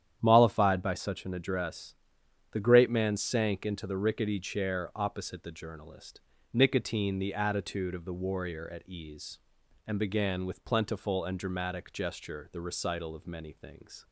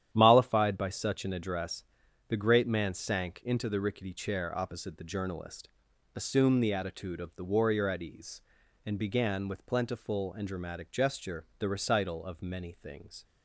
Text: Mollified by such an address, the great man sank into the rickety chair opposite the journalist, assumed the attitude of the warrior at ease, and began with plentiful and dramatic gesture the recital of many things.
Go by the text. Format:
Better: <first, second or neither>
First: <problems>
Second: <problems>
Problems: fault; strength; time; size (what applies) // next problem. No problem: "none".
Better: second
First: starts louder than the rest; strong; until 1.2 s; 9.5 dB // says "nicotine" for "assumed"; at 6.5 s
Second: starts louder than the rest; strong; until 1.1 s; 10.5 dB